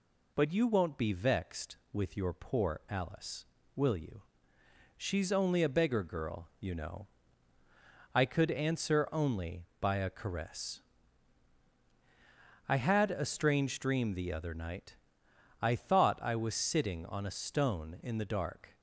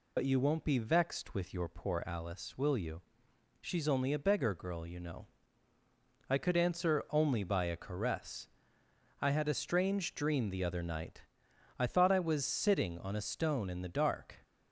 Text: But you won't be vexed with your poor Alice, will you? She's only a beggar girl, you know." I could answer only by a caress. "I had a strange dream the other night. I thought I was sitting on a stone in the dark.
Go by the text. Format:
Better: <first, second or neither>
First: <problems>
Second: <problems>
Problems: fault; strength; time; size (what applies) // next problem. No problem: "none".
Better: first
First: none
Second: loses the start of "But"; at 0.1 s; 65 ms